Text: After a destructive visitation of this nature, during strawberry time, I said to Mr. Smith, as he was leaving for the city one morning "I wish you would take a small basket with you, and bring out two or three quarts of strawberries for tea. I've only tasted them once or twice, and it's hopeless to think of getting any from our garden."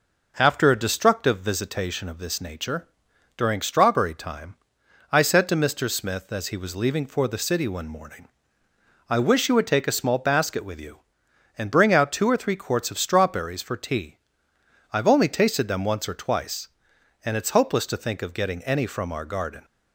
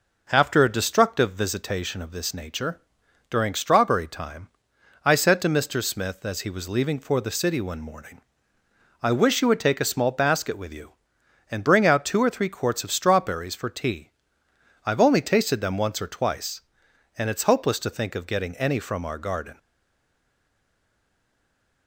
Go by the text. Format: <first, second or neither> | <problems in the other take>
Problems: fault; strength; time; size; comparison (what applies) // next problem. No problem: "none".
first | pauses between "morning" and "I"; noticeable; at 8.1 s; 0.82 s long; noticeable in the first // stays silent after the last word; from 19.5 s on; 2.3 s long